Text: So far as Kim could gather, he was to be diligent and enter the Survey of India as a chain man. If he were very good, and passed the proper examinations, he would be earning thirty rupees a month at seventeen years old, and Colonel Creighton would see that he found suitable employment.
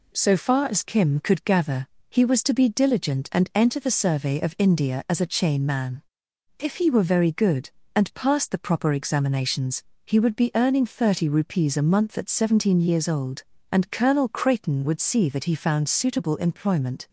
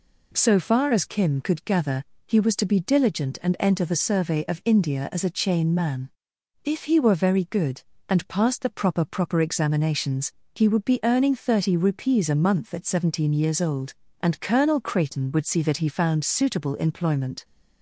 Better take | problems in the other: first | says "proper" twice; at 9.0 s

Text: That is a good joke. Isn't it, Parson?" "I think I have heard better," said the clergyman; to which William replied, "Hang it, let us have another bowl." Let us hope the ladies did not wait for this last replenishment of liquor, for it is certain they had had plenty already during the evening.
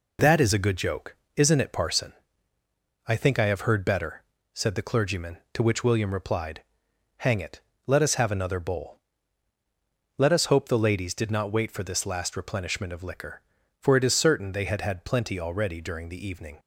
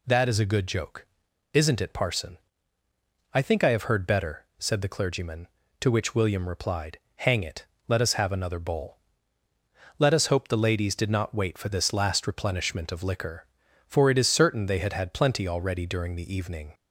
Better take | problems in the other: neither | none

